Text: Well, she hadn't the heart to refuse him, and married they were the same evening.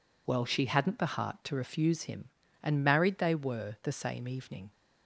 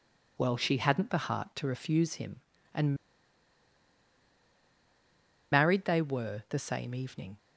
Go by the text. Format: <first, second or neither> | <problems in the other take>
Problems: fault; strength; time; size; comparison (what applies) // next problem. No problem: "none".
first | pauses between "and" and "married"; strong; at 2.9 s; 2.5 s long